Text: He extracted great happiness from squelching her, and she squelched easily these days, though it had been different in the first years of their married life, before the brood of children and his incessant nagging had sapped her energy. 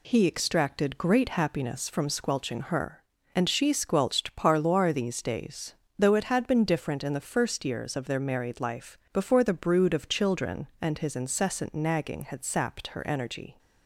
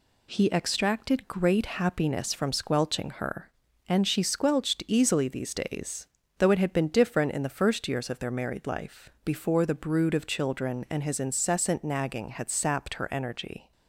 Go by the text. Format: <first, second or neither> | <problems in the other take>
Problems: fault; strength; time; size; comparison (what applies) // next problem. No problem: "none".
second | says "parloir" for "easily"; at 4.3 s